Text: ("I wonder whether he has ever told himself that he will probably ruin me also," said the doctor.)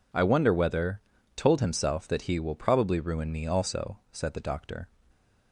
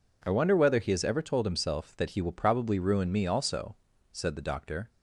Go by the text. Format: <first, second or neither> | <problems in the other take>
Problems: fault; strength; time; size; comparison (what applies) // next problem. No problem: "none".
second | skips "he has ever"; at 1.1 s